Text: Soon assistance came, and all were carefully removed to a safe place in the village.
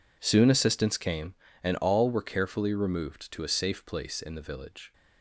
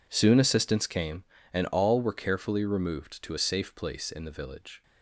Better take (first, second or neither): neither